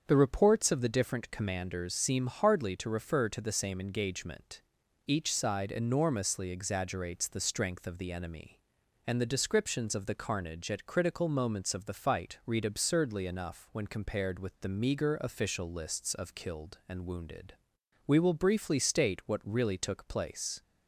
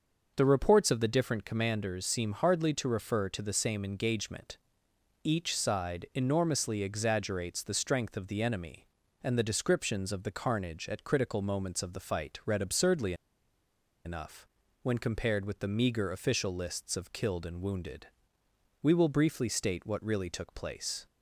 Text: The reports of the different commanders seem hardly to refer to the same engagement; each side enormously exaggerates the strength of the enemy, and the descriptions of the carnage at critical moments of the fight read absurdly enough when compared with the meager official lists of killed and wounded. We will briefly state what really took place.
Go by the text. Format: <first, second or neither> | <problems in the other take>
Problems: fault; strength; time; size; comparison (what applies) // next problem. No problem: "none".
first | starts louder than the rest; until 1.3 s; 6 dB; also in the first // pauses between "absurdly" and "enough"; noticeable; at 13.1 s; 0.91 s long // pauses between "enough" and "when"; slight; at 14.4 s; 0.34 s long